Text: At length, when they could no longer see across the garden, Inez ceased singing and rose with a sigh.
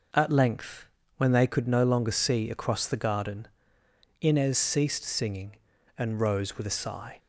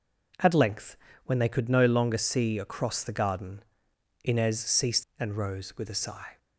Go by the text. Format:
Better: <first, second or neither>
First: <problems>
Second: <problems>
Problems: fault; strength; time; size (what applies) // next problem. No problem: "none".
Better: first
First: none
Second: skips "singing"; at 5.1 s